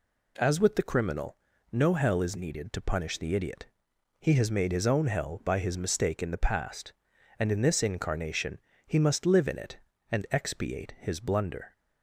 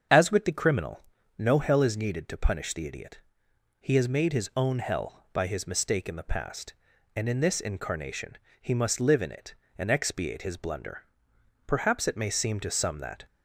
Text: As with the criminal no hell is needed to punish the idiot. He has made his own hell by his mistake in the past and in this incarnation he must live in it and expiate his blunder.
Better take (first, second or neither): first